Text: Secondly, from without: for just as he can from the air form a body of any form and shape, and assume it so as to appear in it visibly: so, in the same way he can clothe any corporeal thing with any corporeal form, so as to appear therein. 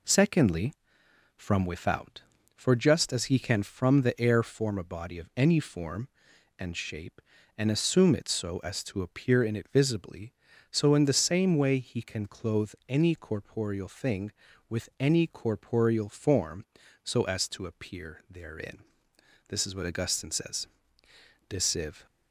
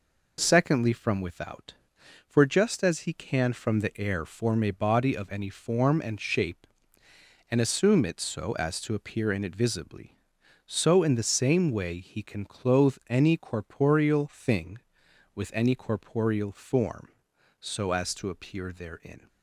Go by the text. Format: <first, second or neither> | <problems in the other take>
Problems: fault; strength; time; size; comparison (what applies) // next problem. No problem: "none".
second | goes on to say "This is what Augustine says De Civ"; strong; from 19.4 s on; 2.5 s long